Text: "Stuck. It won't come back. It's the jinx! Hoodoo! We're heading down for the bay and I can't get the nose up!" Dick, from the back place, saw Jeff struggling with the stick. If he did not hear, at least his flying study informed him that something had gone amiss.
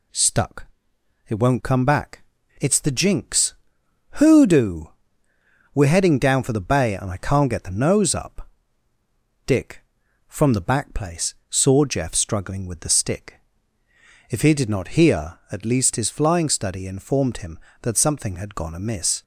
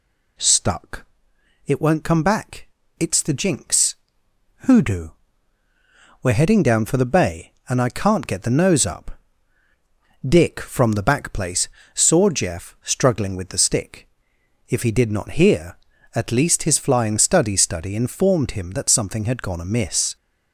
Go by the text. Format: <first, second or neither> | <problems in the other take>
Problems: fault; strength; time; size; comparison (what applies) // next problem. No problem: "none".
first | says "study" twice; at 17.5 s